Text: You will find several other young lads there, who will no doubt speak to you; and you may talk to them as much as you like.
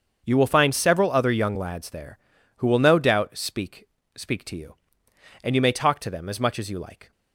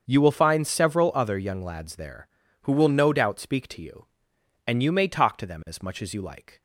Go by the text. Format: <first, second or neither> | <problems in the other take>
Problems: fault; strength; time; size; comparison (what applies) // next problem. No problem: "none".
second | starts louder than the rest; until 1.2 s; 7 dB; also in the second // says "speak" twice; at 4.1 s